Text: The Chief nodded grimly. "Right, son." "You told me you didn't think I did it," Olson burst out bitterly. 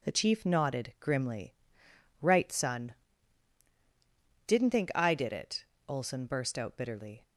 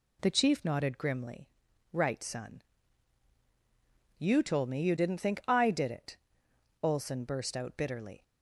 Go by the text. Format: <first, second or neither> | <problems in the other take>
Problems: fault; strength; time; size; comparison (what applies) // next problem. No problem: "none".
second | skips "You told me you"; at 3.7 s